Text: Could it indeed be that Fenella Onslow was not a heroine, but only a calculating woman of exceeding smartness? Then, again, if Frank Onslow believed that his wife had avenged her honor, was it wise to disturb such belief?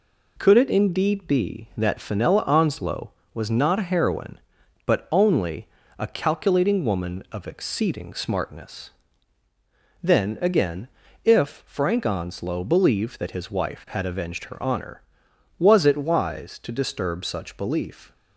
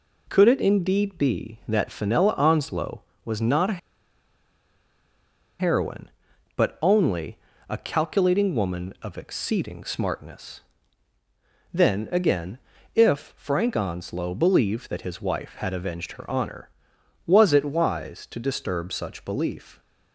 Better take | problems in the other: first | pauses between "a" and "heroine"; strong; at 3.7 s; 1.8 s long // pauses between "only" and "a"; slight; at 7.3 s; 0.30 s long; slight in the first

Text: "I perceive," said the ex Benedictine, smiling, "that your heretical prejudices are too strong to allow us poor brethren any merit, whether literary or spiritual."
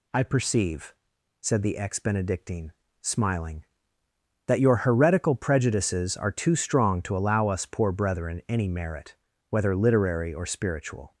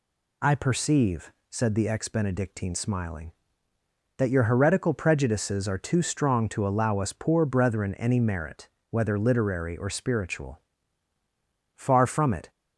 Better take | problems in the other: first | goes on to say "Far from it"; noticeable; from 11.7 s on; 0.76 s long

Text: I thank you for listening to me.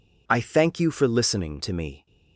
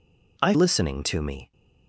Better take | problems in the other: first | skips "thank you for"; at 0.5 s

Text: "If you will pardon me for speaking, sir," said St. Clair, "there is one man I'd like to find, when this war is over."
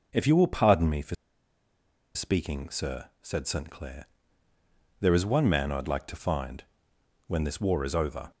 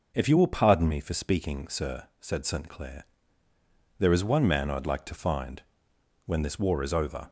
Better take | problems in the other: second | pauses between "for" and "speaking"; at 1.1 s; 1.0 s long

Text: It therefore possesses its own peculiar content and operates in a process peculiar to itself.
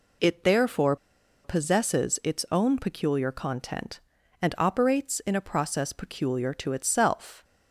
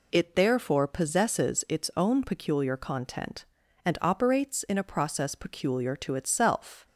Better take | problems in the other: second | pauses between "therefore" and "possesses"; noticeable; at 0.9 s; 0.49 s long

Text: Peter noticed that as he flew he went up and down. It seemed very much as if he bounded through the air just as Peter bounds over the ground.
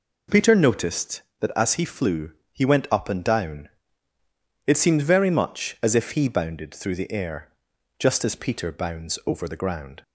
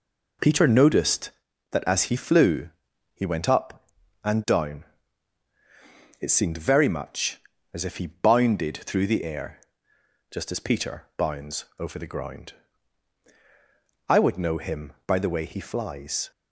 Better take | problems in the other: first | pauses between "flew" and "he"; at 2.6 s; 0.44 s long; slight in the first // pauses between "air" and "just"; noticeable; at 9.5 s; 0.74 s long; noticeable in the first // goes on to say "I would know him by the way he flies"; strong; from 14.0 s on; 2.2 s long

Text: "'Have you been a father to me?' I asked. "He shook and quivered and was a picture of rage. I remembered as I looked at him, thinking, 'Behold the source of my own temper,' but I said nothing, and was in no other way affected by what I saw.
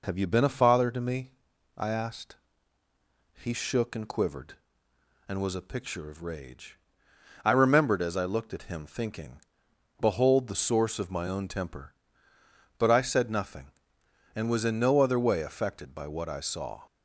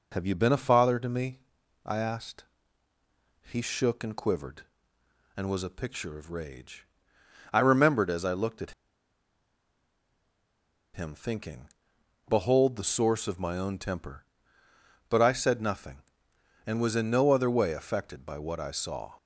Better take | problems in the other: first | pauses between "at" and "him"; strong; at 8.7 s; 2.2 s long

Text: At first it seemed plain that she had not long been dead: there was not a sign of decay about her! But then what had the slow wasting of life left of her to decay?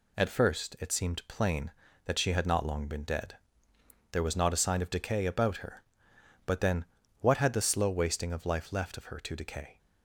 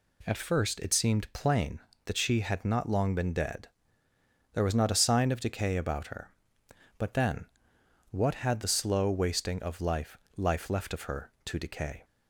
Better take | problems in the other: first | pauses between "then" and "what"; noticeable; at 7.4 s; 0.64 s long; also in the first // says "life" twice; at 10.3 s

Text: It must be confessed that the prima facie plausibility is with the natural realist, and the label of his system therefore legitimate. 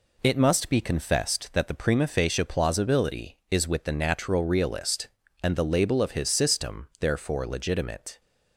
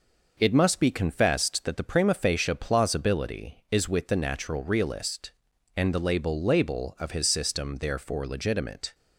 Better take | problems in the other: first | says "label" twice; at 6.4 s

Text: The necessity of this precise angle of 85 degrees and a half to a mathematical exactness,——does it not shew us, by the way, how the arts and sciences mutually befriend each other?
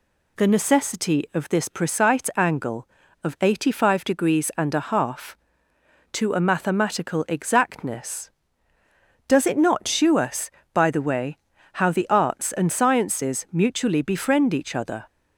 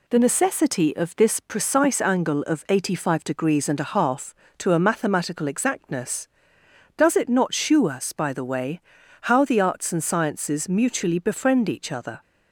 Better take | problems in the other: neither | none

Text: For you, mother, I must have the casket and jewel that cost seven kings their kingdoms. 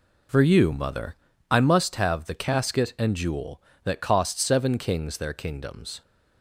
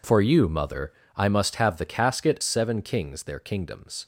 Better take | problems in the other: first | skips "and jewel that cost"; at 2.4 s

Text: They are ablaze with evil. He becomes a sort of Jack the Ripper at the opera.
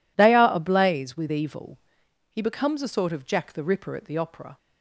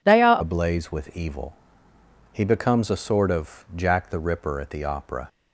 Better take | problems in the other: first | changes voice at "ablaze"; from 0.4 s on; 4.8 s long

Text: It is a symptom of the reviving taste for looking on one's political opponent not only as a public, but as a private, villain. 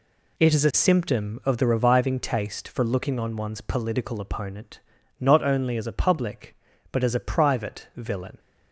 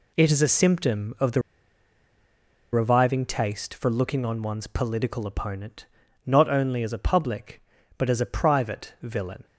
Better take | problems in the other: first | pauses between "the" and "reviving"; strong; at 1.4 s; 1.3 s long // pauses between "opponent" and "not"; at 5.8 s; 0.42 s long; also in the first

